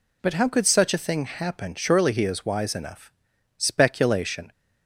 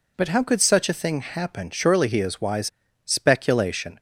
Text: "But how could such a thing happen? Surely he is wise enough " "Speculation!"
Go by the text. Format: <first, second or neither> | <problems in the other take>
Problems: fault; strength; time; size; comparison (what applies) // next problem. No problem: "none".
first | skips "enough"; at 2.7 s